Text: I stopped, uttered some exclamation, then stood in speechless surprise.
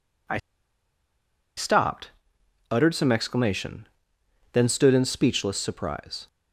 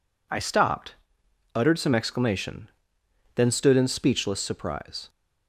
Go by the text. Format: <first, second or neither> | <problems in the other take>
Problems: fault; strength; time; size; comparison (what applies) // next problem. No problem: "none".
second | pauses between "I" and "stopped"; at 0.3 s; 1.1 s long